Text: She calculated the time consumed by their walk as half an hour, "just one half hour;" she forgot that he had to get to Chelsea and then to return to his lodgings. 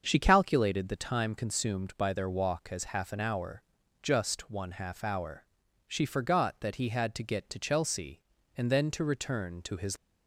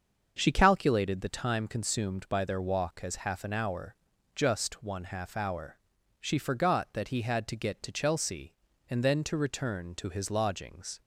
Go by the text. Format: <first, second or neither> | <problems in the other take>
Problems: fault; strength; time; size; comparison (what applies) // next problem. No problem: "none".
second | starts louder than the rest; until 1.0 s; 6.5 dB; also in the second // stops before "lodgings"; at 9.9 s